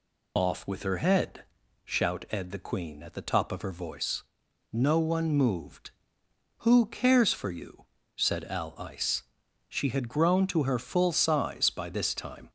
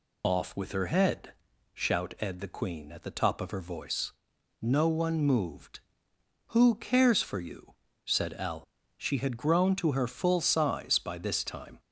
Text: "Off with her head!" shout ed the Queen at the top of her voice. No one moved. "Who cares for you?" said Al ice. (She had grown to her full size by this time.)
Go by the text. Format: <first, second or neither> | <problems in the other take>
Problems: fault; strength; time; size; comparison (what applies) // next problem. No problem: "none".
first | skips "ice"; at 8.7 s